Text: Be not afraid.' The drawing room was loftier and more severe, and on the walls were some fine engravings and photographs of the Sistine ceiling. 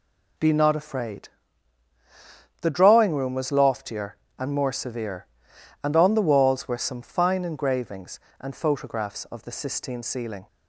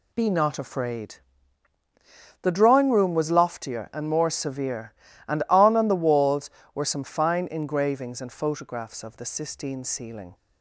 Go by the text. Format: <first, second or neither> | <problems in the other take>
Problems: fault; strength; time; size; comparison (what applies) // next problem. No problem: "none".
first | says "on" twice; at 5.7 s